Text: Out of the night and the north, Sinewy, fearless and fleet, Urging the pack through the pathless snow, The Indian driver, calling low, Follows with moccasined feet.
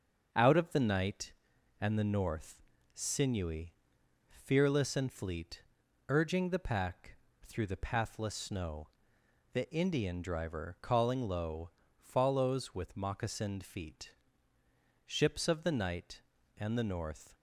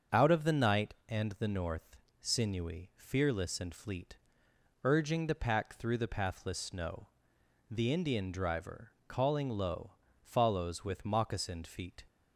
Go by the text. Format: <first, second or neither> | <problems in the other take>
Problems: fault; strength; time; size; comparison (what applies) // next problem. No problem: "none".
second | starts louder than the rest; until 1.3 s; 6.5 dB; also in the second // pauses between "pack" and "through"; slight; at 7.1 s; 0.26 s long // goes on to say "Ships of the night and the north"; strong; from 15.0 s on; 2.2 s long